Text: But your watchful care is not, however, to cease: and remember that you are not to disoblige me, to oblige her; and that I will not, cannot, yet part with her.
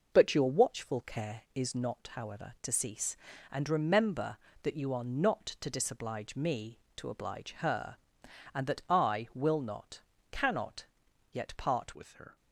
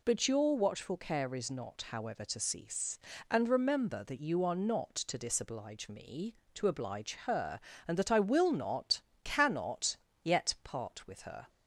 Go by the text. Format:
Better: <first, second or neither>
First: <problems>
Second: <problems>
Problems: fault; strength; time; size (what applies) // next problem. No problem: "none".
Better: second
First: changes voice at "with"; from 11.9 s on; 0.4 s long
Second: none